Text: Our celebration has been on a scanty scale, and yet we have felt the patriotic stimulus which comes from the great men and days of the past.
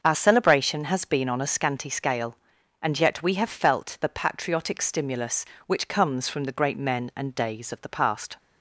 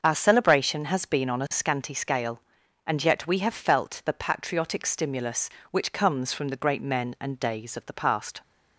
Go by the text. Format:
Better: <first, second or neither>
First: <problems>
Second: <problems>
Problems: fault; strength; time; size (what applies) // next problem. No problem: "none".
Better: neither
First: starts louder than the rest; until 1.0 s; 6.5 dB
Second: starts louder than the rest; until 1.0 s; 6.5 dB